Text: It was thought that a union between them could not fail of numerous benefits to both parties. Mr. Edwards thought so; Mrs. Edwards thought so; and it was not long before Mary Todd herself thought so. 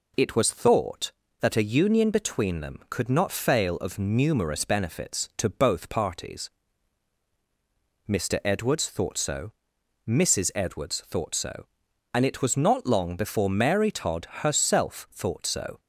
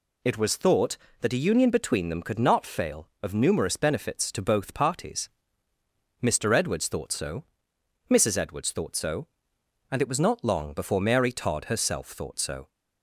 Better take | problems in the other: neither | none

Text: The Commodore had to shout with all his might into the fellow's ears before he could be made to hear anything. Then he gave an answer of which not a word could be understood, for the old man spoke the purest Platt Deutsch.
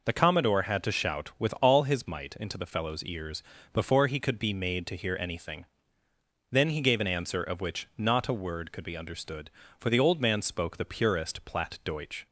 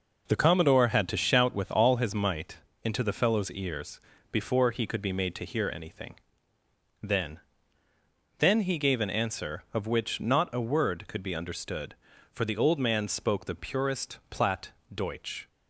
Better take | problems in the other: first | pauses between "might" and "into"; slight; at 2.5 s; 0.26 s long // pauses between "ears" and "before"; slight; at 3.9 s; 0.32 s long; slight in the first // says "Then" twice; at 8.3 s // pauses between "Platt" and "Deutsch"; slight; at 14.7 s; 0.20 s long

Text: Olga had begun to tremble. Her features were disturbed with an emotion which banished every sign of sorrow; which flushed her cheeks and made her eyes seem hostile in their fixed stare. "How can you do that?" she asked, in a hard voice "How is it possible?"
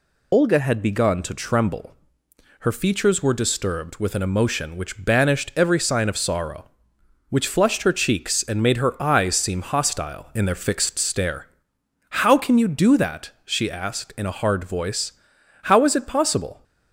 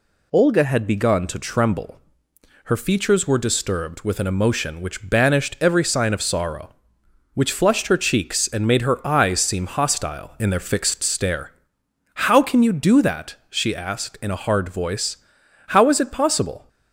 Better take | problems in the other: second | loses the start of "Olga"; at 0.3 s; 50 ms // pauses between "voice" and "How"; noticeable; at 15.1 s; 0.54 s long; noticeable in the second

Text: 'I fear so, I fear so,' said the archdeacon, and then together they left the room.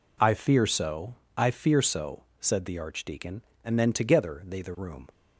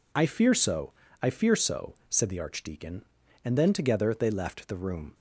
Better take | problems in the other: second | skips "left"; at 4.6 s

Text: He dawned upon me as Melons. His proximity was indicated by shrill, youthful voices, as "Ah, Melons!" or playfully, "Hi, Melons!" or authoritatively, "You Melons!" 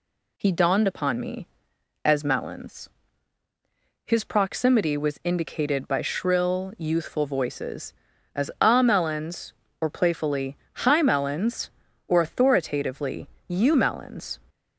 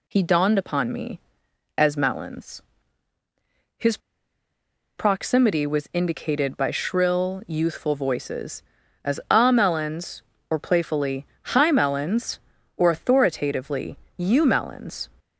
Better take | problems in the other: first | pauses between "His" and "proximity"; at 3.9 s; 0.99 s long

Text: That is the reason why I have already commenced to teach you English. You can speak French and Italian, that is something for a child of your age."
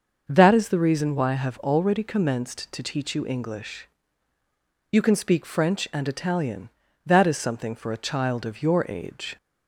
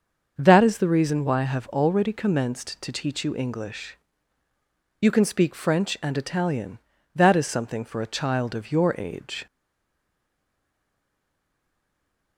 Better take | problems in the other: first | starts louder than the rest; until 1.3 s; 6.5 dB; also in the first // stays silent after the last word; strong; from 9.4 s on; 2.9 s long

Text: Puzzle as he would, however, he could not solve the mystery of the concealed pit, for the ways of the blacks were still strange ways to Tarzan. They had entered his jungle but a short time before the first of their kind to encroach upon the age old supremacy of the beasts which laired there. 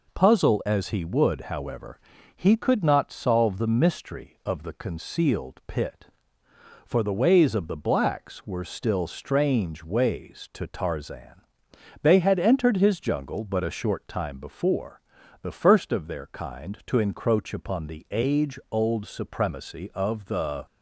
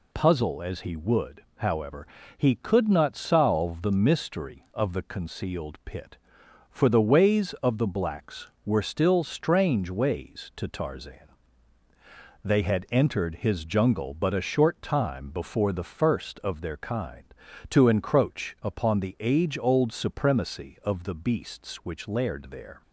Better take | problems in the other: second | pauses between "before" and "the"; at 15.0 s; 0.40 s long // stops before "beasts which laired there"; at 20.6 s

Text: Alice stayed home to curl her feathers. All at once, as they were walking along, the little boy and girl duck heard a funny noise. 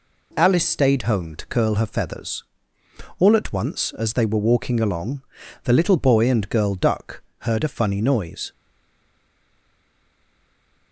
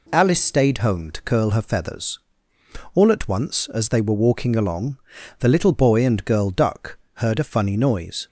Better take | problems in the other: second | pauses between "duck" and "heard"; slight; at 7.2 s; 0.18 s long; slight in the second // stays silent after the last word; from 8.5 s on; 2.4 s long

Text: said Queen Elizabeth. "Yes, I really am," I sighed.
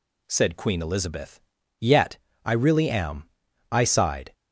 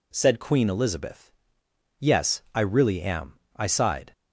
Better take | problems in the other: second | says "Yet" for "Yes"; at 1.7 s

